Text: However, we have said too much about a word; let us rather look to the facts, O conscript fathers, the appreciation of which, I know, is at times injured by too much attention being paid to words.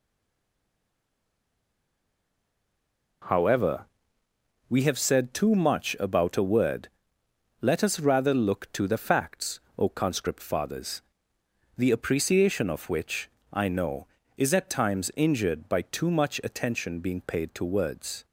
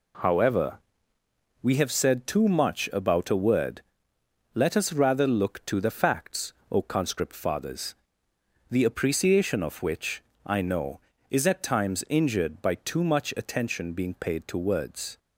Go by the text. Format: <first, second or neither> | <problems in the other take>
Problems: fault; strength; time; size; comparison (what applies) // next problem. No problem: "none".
second | stays silent before the first word; strong; until 3.2 s; 3.2 s long